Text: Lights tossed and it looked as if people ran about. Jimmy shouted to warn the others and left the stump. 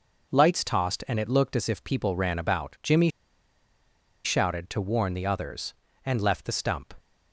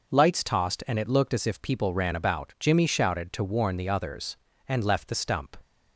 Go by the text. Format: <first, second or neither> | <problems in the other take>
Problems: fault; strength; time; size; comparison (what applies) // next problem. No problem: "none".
second | pauses between "Jimmy" and "shouted"; at 3.0 s; 1.1 s long